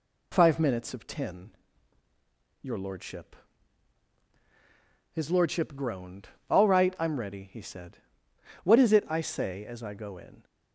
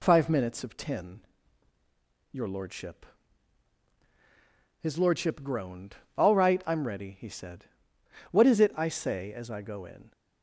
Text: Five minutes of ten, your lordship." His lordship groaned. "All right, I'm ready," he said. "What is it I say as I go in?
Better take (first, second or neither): neither